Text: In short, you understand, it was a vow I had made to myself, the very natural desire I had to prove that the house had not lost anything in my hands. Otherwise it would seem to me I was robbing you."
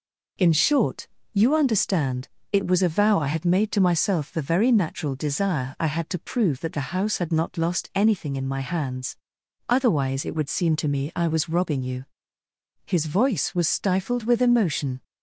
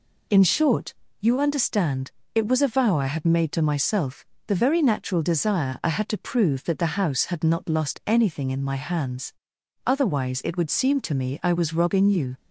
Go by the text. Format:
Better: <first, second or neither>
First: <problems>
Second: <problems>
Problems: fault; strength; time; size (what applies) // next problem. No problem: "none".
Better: second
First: goes on to say "His voice was stifled with emotion"; strong; from 12.8 s on; 2.1 s long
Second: none